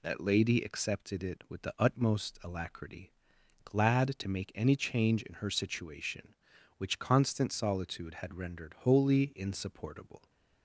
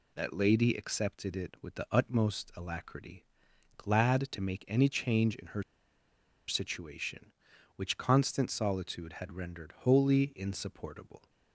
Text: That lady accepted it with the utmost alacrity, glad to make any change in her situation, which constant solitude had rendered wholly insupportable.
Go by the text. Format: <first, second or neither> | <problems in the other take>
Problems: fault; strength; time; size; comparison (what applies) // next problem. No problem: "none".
first | pauses between "her" and "situation"; noticeable; at 5.6 s; 0.85 s long